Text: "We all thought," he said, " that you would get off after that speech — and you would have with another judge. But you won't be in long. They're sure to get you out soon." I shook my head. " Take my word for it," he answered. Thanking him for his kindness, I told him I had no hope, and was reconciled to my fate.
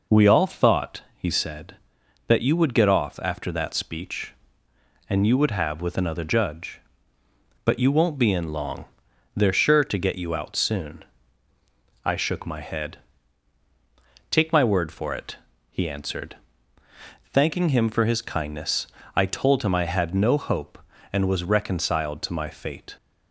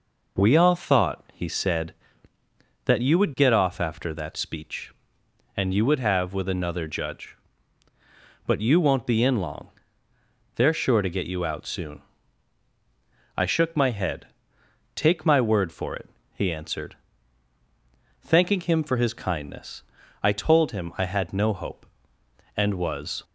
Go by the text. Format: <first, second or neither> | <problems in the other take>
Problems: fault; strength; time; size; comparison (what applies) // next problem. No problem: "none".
first | stops before "reconciled to my fate"; at 23.2 s